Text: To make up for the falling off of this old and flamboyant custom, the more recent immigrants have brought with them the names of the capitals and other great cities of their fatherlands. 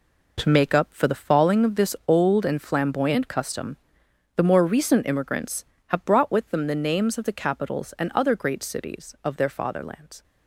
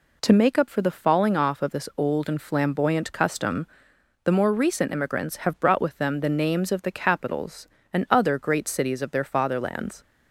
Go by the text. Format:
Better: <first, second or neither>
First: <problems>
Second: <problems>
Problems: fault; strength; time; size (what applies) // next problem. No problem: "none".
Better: second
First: skips "off"; at 1.6 s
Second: none